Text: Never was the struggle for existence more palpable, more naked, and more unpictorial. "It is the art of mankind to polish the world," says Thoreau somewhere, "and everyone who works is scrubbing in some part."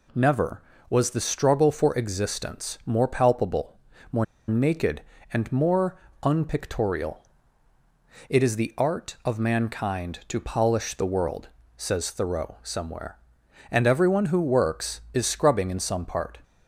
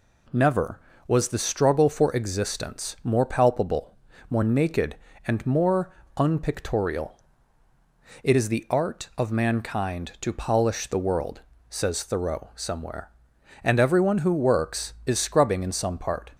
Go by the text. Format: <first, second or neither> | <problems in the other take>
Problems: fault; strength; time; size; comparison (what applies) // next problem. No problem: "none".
second | pauses between "more" and "naked"; slight; at 4.2 s; 0.23 s long // pauses between "more" and "unpictorial"; slight; at 5.9 s; 0.26 s long; slight in the second